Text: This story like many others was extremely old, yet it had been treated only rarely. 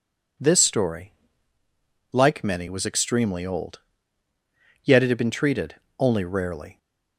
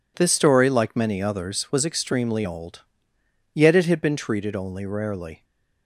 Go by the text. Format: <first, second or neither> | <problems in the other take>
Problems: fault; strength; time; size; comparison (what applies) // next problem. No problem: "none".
second | pauses between "story" and "like"; at 1.1 s; 1.0 s long // skips "others"; at 2.6 s // pauses between "treated" and "only"; slight; at 5.7 s; 0.24 s long